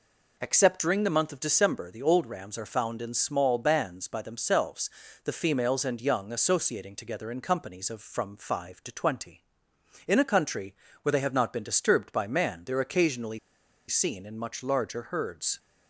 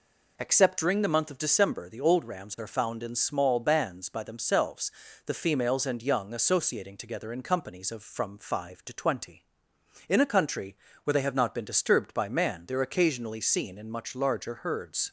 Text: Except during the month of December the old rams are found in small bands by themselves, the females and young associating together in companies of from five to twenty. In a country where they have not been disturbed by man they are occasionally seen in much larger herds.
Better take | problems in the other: second | pauses between "country" and "where"; slight; at 10.7 s; 0.26 s long; slight in the second // pauses between "occasionally" and "seen"; noticeable; at 13.3 s; 0.49 s long

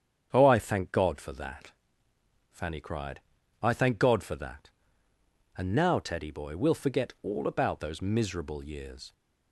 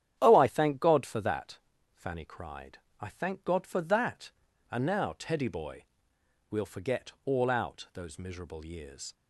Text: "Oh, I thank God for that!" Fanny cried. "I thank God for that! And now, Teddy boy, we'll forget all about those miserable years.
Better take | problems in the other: first | starts louder than the rest; strong; until 1.2 s; 10 dB; strong in the first // says "out" for "about"; at 7.4 s

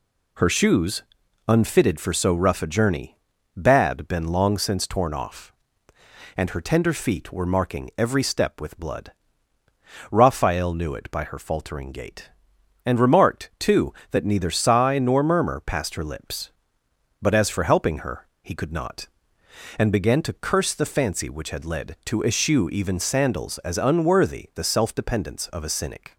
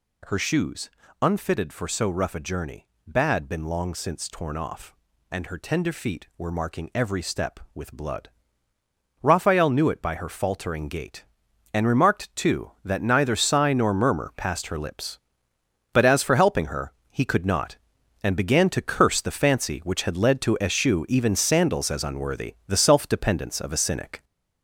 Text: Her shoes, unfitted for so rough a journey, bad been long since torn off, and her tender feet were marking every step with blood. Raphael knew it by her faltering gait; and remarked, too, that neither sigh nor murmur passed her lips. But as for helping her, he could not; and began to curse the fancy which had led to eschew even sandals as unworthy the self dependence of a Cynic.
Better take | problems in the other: first | gets louder; noticeable; throughout; 5.5 dB

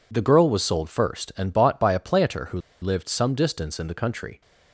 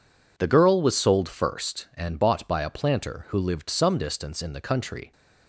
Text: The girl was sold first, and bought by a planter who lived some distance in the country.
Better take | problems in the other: second | pauses between "who" and "lived"; slight; at 2.5 s; 0.21 s long

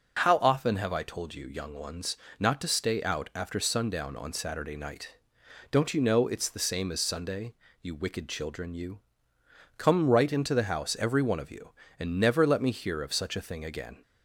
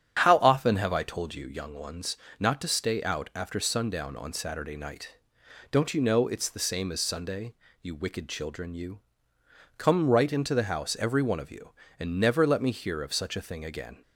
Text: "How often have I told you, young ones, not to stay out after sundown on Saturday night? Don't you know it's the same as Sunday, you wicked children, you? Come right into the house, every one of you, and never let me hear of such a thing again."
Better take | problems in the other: first | starts louder than the rest; strong; until 1.6 s; 8.5 dB

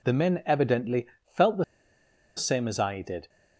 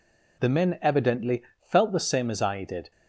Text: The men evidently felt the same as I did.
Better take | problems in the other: second | pauses between "evidently" and "felt"; slight; at 1.0 s; 0.20 s long; slight in the second // pauses between "the" and "same"; noticeable; at 1.6 s; 0.72 s long

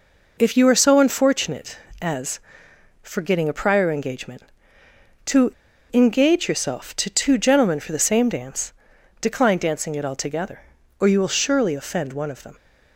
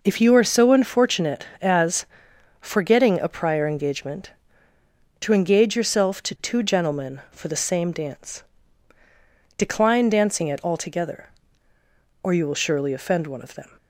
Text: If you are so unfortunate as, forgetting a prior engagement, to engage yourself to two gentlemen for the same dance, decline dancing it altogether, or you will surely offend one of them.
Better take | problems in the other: second | pauses between "to" and "engage"; at 5.5 s; 0.41 s long

